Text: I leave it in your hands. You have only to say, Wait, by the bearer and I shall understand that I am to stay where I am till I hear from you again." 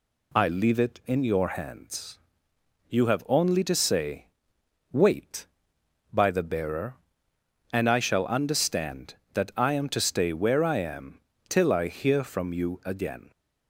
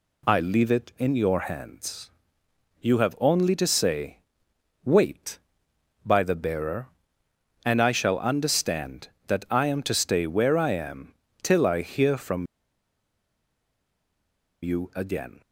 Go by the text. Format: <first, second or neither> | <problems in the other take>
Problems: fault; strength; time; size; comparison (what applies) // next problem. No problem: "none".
first | pauses between "am" and "till"; slight; at 11.1 s; 0.28 s long; slight in the first // pauses between "from" and "you"; strong; at 12.4 s; 2.1 s long